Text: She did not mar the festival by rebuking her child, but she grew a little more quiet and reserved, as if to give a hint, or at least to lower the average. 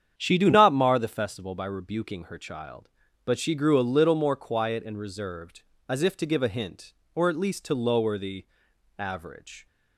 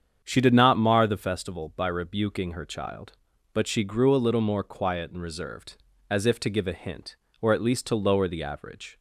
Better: second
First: starts louder than the rest; strong; until 1.1 s; 8.5 dB // says "do" for "did"; at 0.3 s // pauses between "the" and "average"; noticeable; at 8.4 s; 0.52 s long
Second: starts louder than the rest; strong; until 1.2 s; 8 dB

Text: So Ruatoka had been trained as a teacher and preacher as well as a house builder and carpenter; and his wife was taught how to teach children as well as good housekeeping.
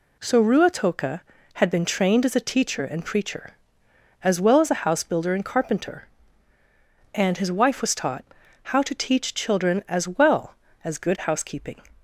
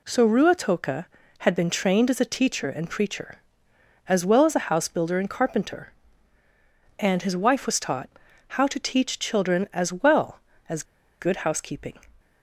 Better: first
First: pauses between "taught" and "how"; at 8.2 s; 0.40 s long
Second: pauses between "taught" and "how"; at 8.0 s; 0.40 s long // pauses between "as" and "good"; at 10.8 s; 0.37 s long

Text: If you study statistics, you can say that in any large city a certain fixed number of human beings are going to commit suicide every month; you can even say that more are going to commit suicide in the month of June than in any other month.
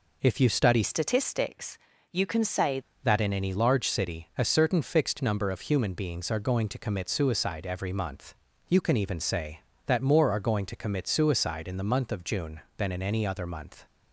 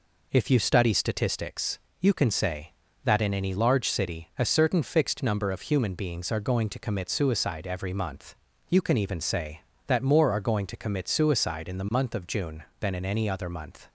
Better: second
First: changes voice from "statistics" to "say"; from 0.8 to 2.8 s; 2.0 s long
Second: none

